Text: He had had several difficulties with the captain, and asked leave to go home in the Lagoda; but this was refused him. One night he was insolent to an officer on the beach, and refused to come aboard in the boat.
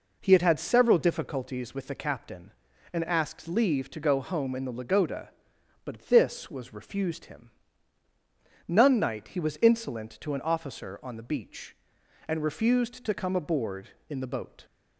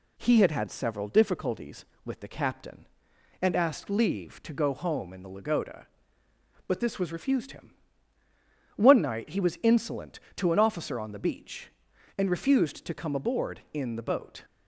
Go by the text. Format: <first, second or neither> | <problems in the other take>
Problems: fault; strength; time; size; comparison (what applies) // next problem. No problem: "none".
second | says "None" for "One"; at 8.6 s